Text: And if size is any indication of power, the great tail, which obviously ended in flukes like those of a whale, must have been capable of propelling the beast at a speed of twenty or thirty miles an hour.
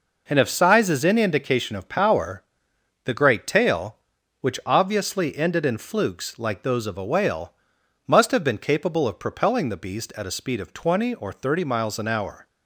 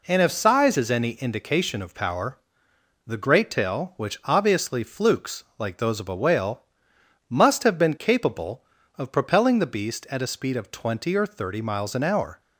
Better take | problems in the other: first | skips "ended in"; at 4.8 s

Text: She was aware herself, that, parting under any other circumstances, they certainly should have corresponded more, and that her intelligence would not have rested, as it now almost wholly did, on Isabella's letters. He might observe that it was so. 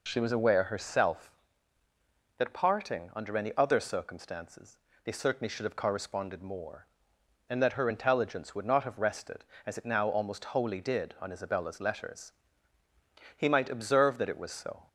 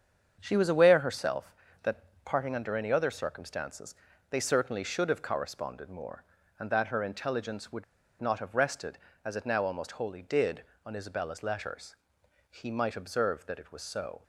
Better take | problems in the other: first | starts louder than the rest; strong; until 1.4 s; 7.5 dB // pauses between "would" and "not"; at 7.8 s; 0.36 s long

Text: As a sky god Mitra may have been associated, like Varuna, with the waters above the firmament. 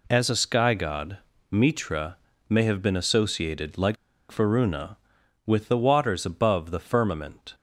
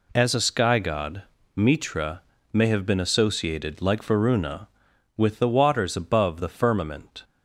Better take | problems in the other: second | pauses between "god" and "Mitra"; slight; at 1.1 s; 0.32 s long; slight in the second // pauses between "Mitra" and "may"; slight; at 2.1 s; 0.30 s long; slight in the second // pauses between "like" and "Varuna"; slight; at 3.9 s; 0.34 s long

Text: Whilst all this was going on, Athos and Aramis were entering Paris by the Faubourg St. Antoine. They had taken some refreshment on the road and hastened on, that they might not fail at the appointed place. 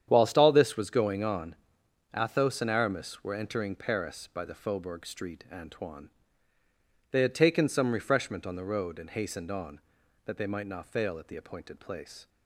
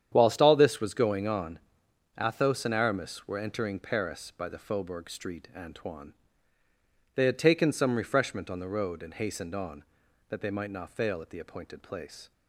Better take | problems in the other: neither | starts louder than the rest; strong; the same in both

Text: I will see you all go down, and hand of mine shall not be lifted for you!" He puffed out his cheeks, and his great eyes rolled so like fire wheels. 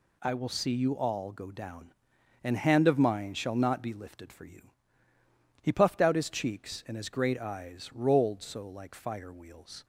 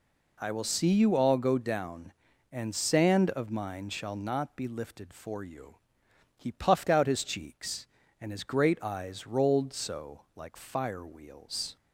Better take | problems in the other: first | says "sand" for "hand"; at 2.7 s // pauses between "so" and "like"; slight; at 10.2 s; 0.16 s long

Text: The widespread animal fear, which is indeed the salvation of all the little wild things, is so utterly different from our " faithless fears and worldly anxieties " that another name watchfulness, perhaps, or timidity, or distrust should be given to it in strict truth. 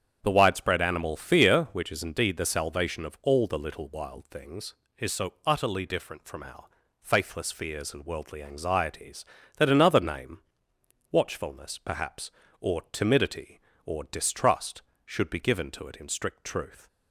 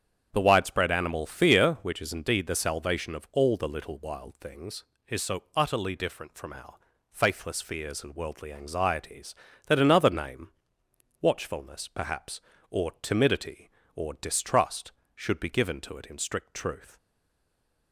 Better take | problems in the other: first | starts louder than the rest; strong; until 1.3 s; 8 dB; strong in the first // pauses between "name" and "watchfulness"; noticeable; at 10.5 s; 0.70 s long; noticeable in the first // stays silent after the last word; slight; from 16.9 s on; 1.0 s long

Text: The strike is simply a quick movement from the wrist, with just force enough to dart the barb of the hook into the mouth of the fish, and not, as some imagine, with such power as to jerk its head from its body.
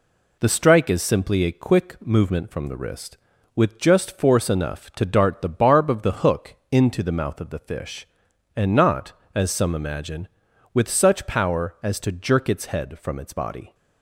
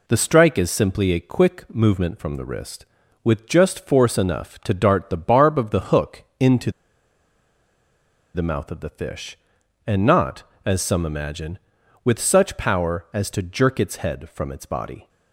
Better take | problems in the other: first | pauses between "into" and "the"; strong; at 6.7 s; 1.6 s long

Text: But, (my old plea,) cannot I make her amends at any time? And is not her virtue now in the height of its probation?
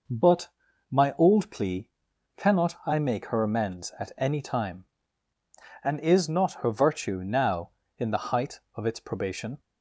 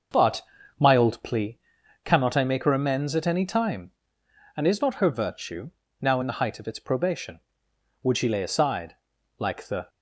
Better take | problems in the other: first | starts louder than the rest; noticeable; until 1.4 s; 6 dB // pauses between "virtue" and "now"; slight; at 5.7 s; 0.32 s long // goes on to say "Would she lay aside like the"; strong; from 8.0 s on; 1.8 s long

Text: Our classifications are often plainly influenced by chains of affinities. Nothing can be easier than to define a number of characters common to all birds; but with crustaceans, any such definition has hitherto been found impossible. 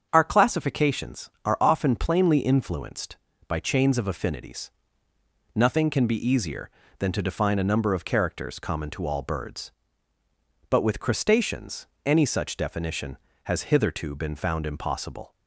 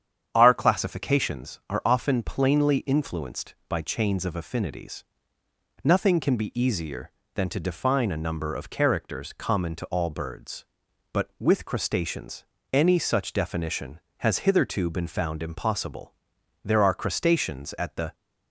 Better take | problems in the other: first | starts louder than the rest; strong; until 1.3 s; 8.5 dB; strong in the first // goes on to say "There are crustaceans at the"; from 16.6 s on; 1.5 s long

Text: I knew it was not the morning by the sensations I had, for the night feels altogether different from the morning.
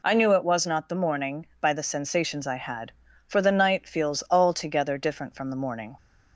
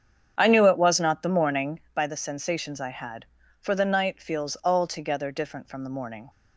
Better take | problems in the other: first | starts louder than the rest; strong; until 2.0 s; 8 dB

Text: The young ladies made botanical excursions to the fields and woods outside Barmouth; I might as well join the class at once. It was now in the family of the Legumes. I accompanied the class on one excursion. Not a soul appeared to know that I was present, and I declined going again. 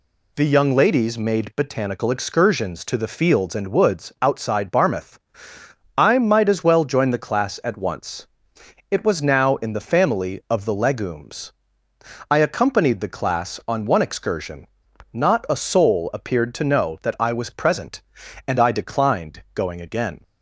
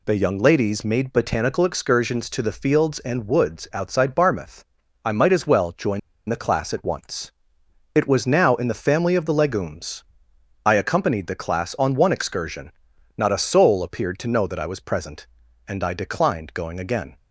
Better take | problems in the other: first | pauses between "join" and "the"; slight; at 5.9 s; 0.28 s long

